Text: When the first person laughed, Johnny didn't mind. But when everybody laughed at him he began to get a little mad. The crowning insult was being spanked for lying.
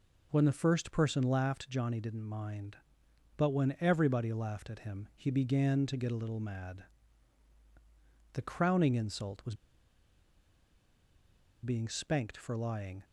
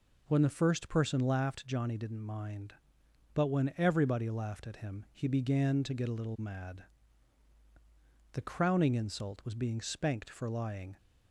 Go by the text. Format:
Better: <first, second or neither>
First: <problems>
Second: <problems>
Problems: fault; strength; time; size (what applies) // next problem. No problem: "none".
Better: second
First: pauses between "was" and "being"; strong; at 9.5 s; 2.0 s long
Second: none